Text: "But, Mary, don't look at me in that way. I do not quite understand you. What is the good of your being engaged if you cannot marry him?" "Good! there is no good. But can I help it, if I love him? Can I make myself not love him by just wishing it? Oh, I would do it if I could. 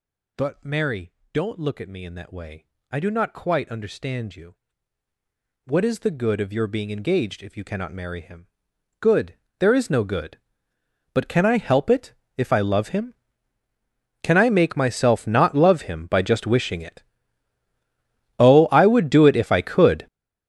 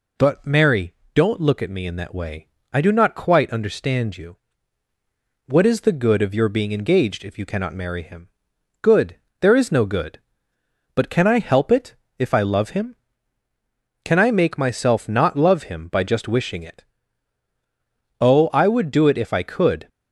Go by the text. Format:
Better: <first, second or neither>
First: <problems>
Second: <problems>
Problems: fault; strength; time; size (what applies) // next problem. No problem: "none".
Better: second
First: gets louder; strong; throughout; 14.5 dB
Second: none